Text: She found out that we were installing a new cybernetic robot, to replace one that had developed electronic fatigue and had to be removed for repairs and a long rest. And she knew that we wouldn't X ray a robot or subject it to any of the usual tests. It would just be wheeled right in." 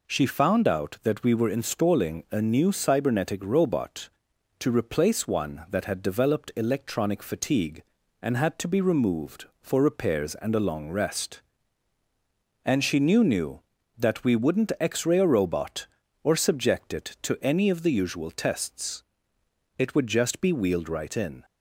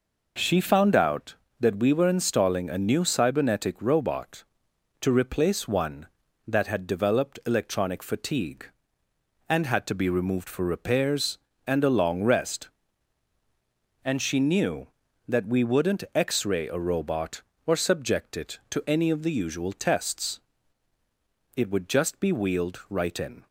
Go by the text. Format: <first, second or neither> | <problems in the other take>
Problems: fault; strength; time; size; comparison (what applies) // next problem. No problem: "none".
second | says "knew" twice; at 13.2 s